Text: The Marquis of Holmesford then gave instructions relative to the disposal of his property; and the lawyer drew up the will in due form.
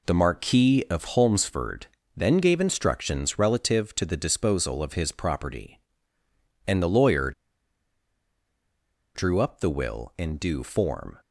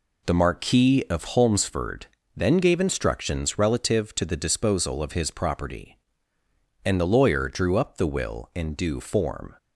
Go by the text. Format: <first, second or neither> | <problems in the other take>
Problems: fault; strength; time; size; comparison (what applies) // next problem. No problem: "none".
second | pauses between "Holmesford" and "then"; slight; at 1.8 s; 0.32 s long; slight in the second // pauses between "lawyer" and "drew"; strong; at 7.3 s; 1.8 s long